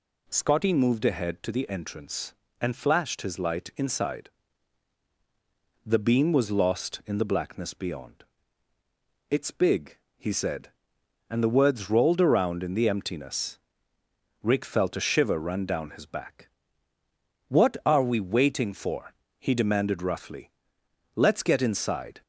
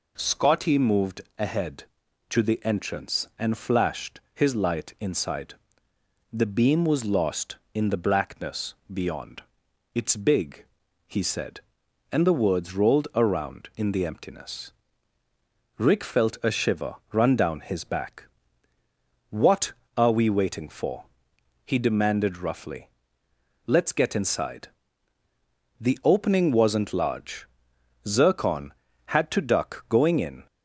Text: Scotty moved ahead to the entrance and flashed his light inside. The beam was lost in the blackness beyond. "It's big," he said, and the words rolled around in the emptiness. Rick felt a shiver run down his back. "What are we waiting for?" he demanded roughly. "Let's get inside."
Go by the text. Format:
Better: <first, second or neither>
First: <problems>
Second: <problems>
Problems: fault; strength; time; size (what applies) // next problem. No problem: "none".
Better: first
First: none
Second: pauses between "moved" and "ahead"; slight; at 1.2 s; 0.18 s long // pauses between "blackness" and "beyond"; slight; at 8.7 s; 0.18 s long // pauses between "shiver" and "run"; slight; at 16.9 s; 0.16 s long // goes on to say "The opening wasn't large Zircon had to duck going in"; strong; from 25.7 s on; 4.6 s long